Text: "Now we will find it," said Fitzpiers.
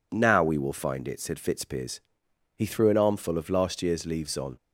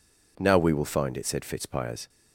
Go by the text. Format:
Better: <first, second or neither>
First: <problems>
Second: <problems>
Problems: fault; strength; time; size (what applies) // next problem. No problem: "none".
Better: second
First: goes on to say "He threw an armful of last year's leaves on"; strong; from 2.5 s on; 2.0 s long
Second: none